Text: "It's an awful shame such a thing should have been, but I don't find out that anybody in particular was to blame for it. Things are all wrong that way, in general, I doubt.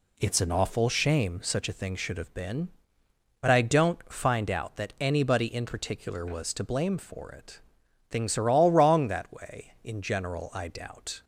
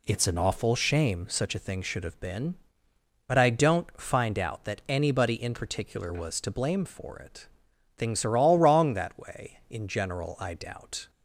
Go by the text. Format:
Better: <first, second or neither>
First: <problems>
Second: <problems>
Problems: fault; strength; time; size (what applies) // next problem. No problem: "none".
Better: neither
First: none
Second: none